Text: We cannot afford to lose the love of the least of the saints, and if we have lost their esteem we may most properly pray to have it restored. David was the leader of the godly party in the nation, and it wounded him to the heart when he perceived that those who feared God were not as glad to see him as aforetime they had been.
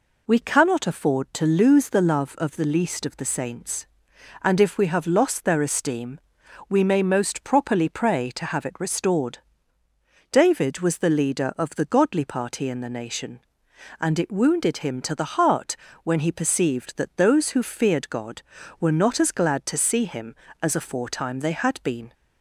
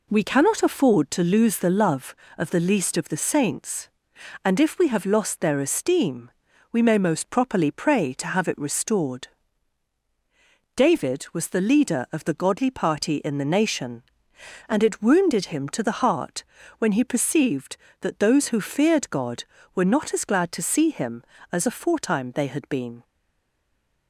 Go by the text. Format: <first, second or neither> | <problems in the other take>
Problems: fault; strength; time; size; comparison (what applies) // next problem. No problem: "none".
first | pauses between "esteem" and "we"; at 6.3 s; 0.40 s long; noticeable in the first // pauses between "heart" and "when"; slight; at 16.4 s; 0.36 s long; slight in the first // stays silent after the last word; from 23.0 s on; 1.0 s long